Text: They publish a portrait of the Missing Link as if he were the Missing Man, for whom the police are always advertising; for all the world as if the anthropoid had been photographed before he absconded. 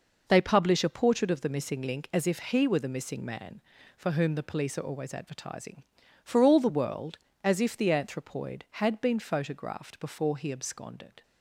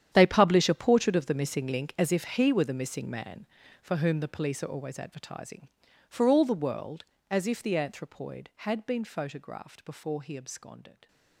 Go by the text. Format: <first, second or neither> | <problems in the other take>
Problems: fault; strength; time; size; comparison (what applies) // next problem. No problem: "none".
first | gets quieter; strong; throughout; 16 dB